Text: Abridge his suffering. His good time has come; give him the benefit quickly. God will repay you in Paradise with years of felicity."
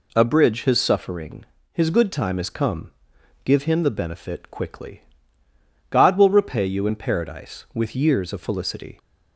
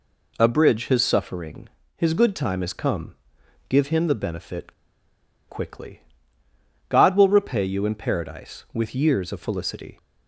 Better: first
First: none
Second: pauses between "benefit" and "quickly"; noticeable; at 4.7 s; 0.75 s long

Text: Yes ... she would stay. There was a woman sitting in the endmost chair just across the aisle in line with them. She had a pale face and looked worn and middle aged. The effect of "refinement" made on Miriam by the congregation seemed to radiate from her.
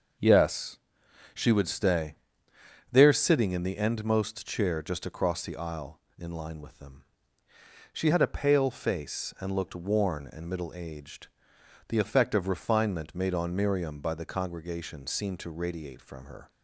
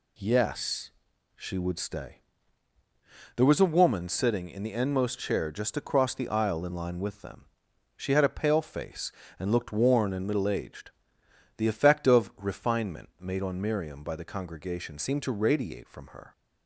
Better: second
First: skips "was a woman"; at 3.1 s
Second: none

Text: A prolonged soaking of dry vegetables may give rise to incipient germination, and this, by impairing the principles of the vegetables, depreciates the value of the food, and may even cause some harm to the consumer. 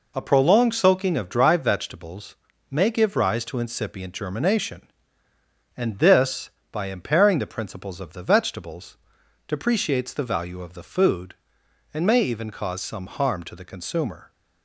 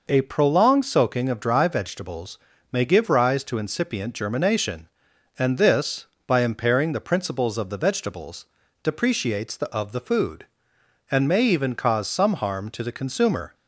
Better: first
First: pauses between "vegetables" and "may"; at 2.3 s; 0.38 s long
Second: pauses between "vegetables" and "may"; slight; at 2.3 s; 0.32 s long // skips "value"; at 9.6 s

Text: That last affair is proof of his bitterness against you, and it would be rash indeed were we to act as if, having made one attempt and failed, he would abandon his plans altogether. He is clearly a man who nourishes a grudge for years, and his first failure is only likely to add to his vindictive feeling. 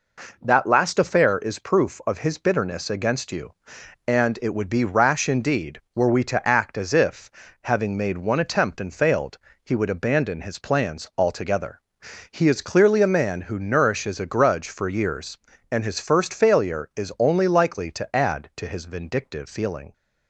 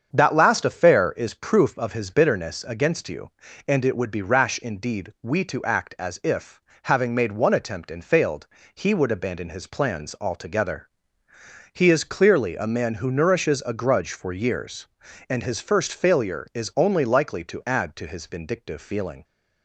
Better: first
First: none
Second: starts louder than the rest; strong; until 1.1 s; 7.5 dB // skips "were"; at 5.1 s

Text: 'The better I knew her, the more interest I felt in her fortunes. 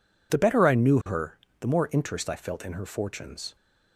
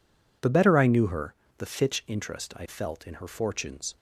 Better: first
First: none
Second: says "fitch" for "more"; at 1.6 s

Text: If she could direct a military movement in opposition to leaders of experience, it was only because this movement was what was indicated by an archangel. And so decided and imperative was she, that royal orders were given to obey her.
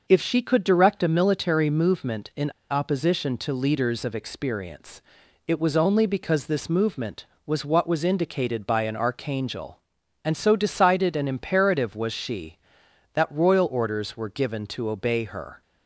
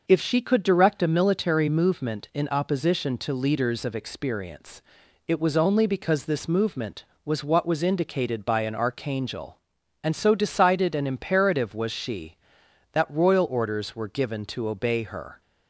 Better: second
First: pauses between "in" and "opposition"; slight; at 2.4 s; 0.20 s long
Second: none

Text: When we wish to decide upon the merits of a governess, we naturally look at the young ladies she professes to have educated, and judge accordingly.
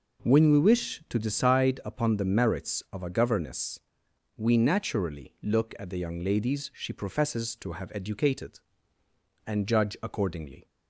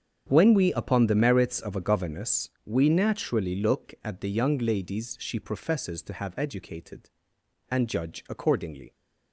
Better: first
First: none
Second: starts louder than the rest; strong; until 1.3 s; 8 dB // skips "wish to decide"; at 0.7 s

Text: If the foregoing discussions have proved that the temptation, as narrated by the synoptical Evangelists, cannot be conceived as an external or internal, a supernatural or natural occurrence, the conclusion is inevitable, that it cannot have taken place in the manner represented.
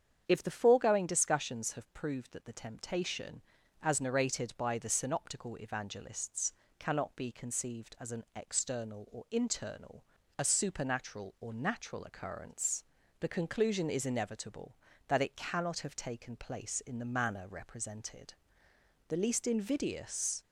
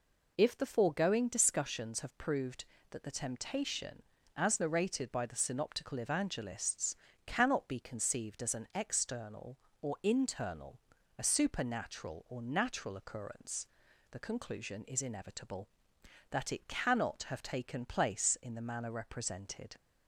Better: second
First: starts louder than the rest; strong; until 1.2 s; 8 dB // goes on to say "The least invidious"; from 19.0 s on; 1.3 s long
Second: none

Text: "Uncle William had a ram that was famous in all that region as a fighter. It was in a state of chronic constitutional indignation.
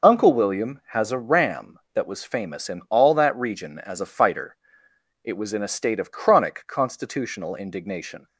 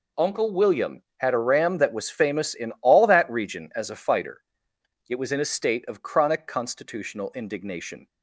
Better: second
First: says "has" for "had"; at 0.9 s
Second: none

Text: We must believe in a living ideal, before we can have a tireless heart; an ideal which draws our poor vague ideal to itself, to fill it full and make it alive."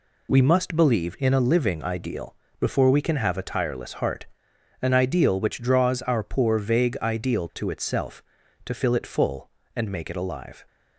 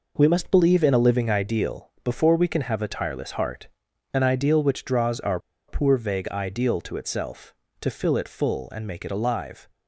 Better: first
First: none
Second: pauses between "our" and "poor"; slight; at 5.3 s; 0.29 s long

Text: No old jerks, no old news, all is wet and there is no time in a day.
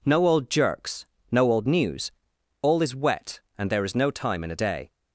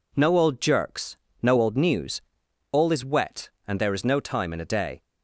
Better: neither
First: none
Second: none

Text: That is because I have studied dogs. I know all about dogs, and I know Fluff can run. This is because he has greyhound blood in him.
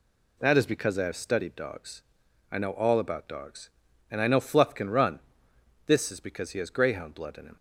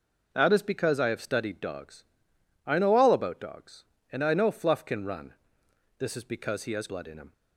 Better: first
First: none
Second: skips "greyhound"; at 6.8 s

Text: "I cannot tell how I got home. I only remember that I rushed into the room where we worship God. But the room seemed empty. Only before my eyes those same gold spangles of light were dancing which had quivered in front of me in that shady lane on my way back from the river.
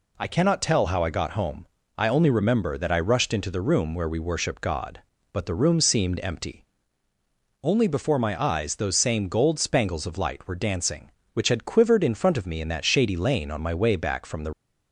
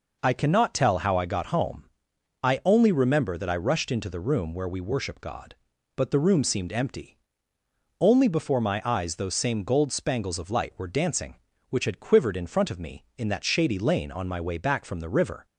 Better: second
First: stops before "river"; at 14.5 s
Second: none

